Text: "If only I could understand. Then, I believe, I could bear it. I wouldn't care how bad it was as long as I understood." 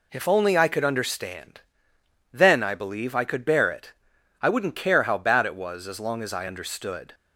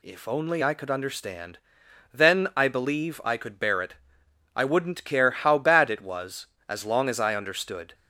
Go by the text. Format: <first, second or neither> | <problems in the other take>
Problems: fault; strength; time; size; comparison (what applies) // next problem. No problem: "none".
second | starts louder than the rest; slight; until 1.3 s; 3 dB